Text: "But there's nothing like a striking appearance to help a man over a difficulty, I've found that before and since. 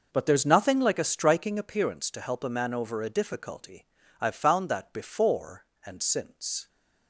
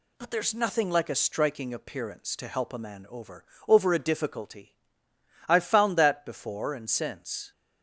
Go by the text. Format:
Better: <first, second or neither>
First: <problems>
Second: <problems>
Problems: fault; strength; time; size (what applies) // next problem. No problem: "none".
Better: first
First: none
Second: says "over" twice; at 3.6 s